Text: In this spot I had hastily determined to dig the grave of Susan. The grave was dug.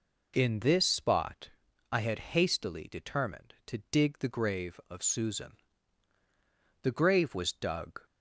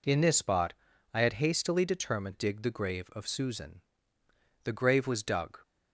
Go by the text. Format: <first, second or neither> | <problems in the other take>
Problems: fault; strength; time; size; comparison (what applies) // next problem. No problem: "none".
first | pauses between "spot" and "I"; at 0.7 s; 0.40 s long; also in the first // skips "to"; at 2.3 s